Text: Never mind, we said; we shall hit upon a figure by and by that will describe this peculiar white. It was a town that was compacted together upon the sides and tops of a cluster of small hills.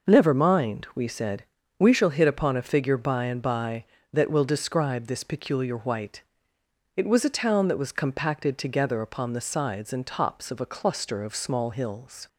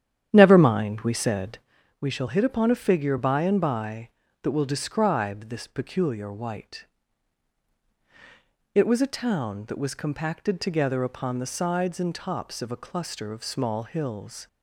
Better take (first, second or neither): first